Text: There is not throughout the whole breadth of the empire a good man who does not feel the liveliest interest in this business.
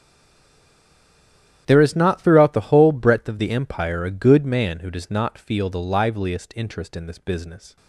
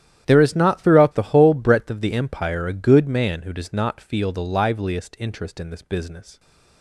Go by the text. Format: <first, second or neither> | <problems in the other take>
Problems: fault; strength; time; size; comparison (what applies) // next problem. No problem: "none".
second | stays silent before the first word; noticeable; until 1.6 s; 1.6 s long // starts louder than the rest; strong; until 2.6 s; 11 dB; strong in the second